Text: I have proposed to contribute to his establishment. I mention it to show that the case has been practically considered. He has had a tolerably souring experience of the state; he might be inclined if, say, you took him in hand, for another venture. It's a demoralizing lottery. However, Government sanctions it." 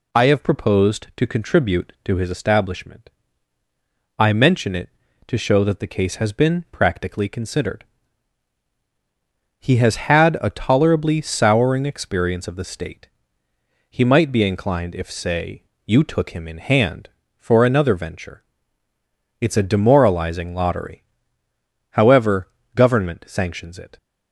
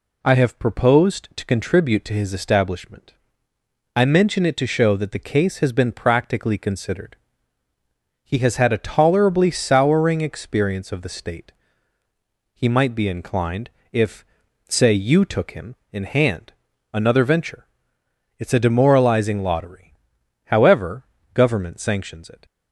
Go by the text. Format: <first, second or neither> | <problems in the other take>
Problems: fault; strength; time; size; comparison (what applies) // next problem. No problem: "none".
first | pauses between "inclined" and "if"; slight; at 13.7 s; 0.20 s long // skips "for"; at 16.7 s